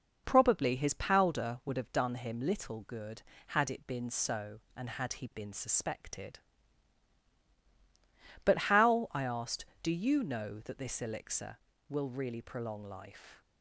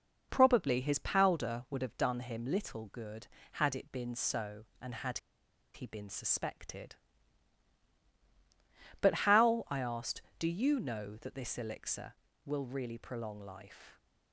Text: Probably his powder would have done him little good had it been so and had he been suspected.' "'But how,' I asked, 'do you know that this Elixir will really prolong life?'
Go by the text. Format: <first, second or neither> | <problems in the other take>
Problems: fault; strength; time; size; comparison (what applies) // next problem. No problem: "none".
first | pauses between "had" and "he"; noticeable; at 5.1 s; 0.55 s long